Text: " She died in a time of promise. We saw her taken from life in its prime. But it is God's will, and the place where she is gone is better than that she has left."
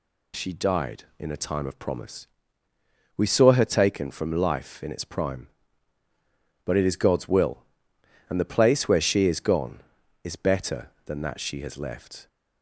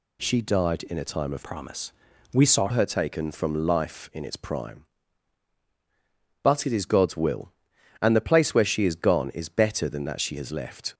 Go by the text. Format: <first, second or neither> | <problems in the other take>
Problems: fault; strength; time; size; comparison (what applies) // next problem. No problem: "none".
first | changes voice from "promise" to "saw"; from 1.4 to 2.6 s; 1.2 s long